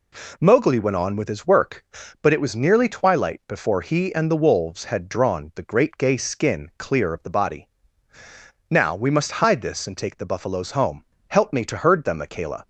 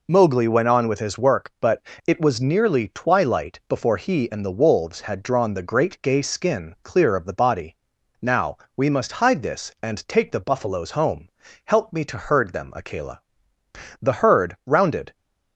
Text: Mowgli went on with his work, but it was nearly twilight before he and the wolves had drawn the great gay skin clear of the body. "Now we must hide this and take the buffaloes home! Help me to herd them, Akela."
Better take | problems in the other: first | pauses between "but" and "it"; slight; at 1.7 s; 0.26 s long // pauses between "Now" and "we"; slight; at 8.5 s; 0.18 s long // goes on to say "The herd rounded"; noticeable; from 14.0 s on; 1.1 s long

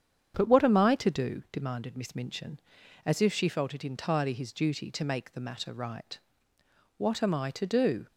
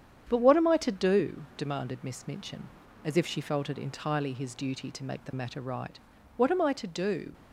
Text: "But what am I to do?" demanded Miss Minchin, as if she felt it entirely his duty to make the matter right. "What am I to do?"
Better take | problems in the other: neither | starts louder than the rest; strong; the same in both

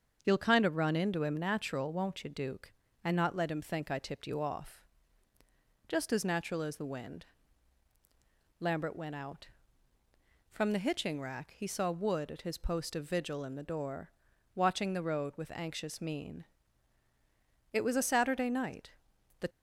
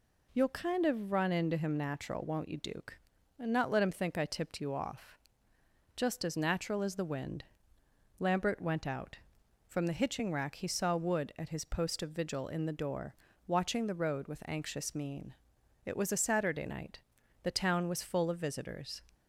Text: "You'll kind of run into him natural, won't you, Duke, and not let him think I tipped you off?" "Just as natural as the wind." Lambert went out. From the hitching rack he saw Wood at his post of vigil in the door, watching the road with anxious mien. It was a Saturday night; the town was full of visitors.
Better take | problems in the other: second | starts louder than the rest; until 1.2 s; 7 dB // stops before "town was full of visitors"; at 19.5 s

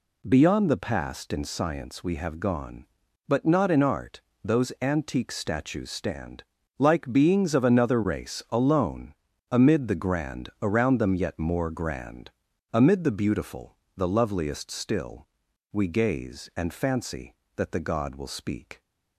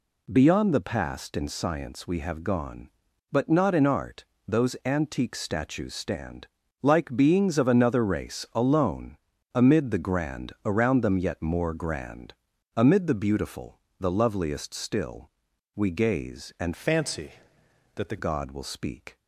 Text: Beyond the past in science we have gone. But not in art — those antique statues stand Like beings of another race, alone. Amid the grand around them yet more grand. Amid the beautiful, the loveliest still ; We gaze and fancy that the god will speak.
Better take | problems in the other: first | pauses between "stand" and "Like"; slight; at 6.4 s; 0.34 s long; slight in the first // changes voice from "fancy" to "the"; from 16.7 to 18.1 s; 1.4 s long

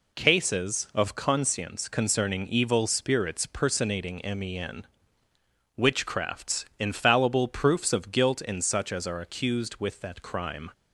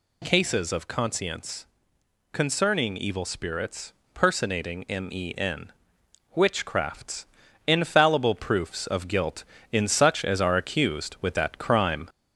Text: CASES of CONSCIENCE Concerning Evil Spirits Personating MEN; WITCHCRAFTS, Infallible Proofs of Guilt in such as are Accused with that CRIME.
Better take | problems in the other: first | gets louder; slight; throughout; 2 dB // pauses between "CONSCIENCE" and "Concerning"; noticeable; at 1.6 s; 0.64 s long // pauses between "Spirits" and "Personating"; slight; at 3.9 s; 0.22 s long

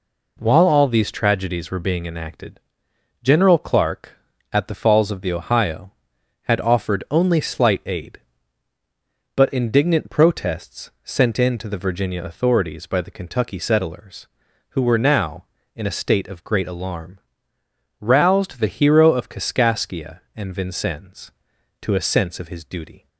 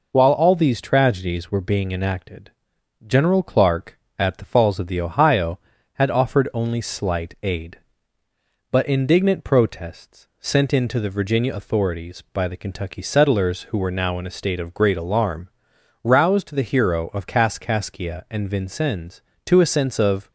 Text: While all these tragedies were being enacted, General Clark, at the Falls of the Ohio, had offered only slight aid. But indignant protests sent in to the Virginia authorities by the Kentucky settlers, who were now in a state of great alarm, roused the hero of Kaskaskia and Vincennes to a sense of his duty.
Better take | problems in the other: first | stops before "his duty"; at 20.2 s

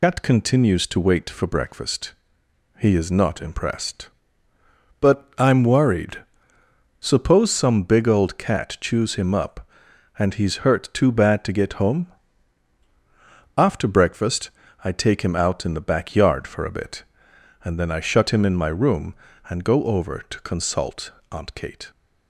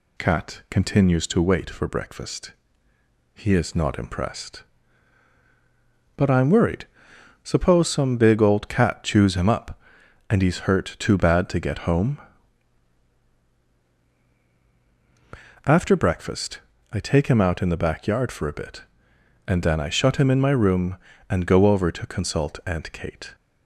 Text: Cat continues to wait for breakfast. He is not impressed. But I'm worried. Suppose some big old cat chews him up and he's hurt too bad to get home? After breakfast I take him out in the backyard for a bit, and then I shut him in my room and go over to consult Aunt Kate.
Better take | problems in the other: second | loses the start of "Cat"; at 0.0 s; 65 ms // pauses between "breakfast" and "I"; slight; at 14.5 s; 0.32 s long; slight in the second // pauses between "consult" and "Aunt"; slight; at 21.1 s; 0.22 s long

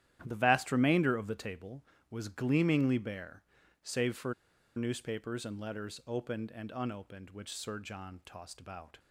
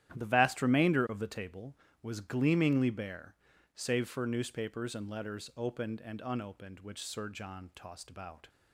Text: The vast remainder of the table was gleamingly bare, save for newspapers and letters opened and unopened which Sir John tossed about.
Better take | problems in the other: second | starts louder than the rest; strong; until 1.2 s; 11.5 dB; strong in the second // pauses between "for" and "newspapers"; at 4.3 s; 0.43 s long

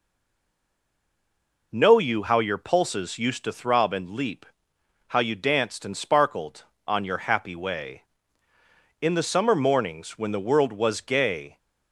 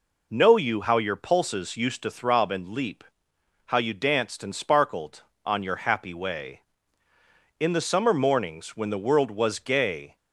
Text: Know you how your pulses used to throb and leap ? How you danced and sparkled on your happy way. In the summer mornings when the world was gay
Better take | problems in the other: second | stays silent before the first word; noticeable; until 1.7 s; 1.7 s long

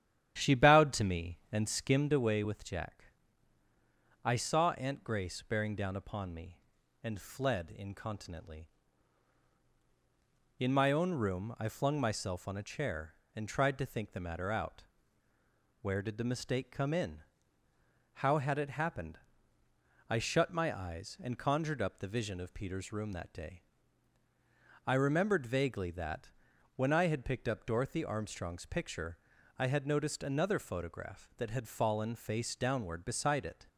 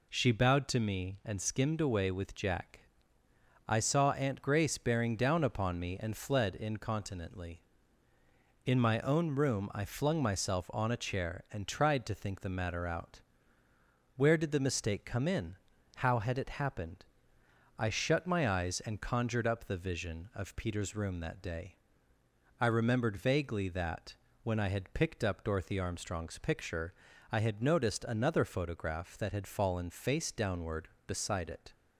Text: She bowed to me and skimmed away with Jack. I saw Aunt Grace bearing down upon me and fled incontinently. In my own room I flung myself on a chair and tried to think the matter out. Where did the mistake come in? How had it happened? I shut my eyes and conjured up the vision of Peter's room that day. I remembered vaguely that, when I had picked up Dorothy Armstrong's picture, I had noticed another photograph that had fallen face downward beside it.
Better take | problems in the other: second | starts louder than the rest; strong; until 2.2 s; 11 dB

